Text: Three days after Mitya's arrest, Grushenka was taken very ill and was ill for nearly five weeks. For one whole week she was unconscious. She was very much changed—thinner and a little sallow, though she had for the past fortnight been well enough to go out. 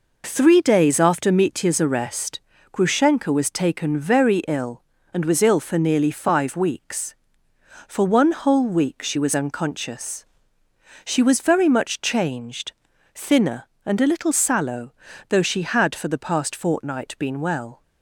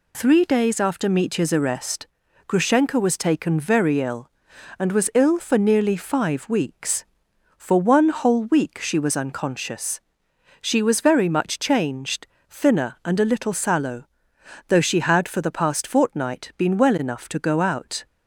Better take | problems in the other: second | stops before "enough to go out"; at 17.8 s

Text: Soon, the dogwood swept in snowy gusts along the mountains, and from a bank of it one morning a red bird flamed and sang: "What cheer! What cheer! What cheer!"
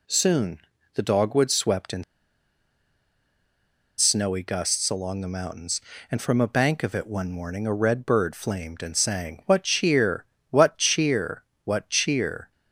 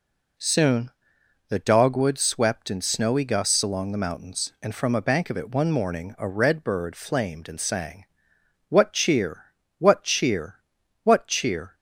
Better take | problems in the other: second | pauses between "in" and "snowy"; strong; at 2.0 s; 1.9 s long

